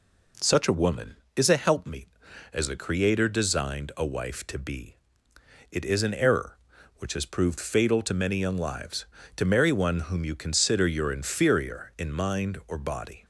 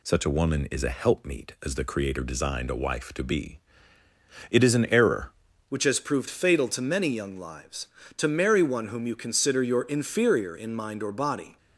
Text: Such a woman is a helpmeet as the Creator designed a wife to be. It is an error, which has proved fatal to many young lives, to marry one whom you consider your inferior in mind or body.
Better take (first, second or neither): first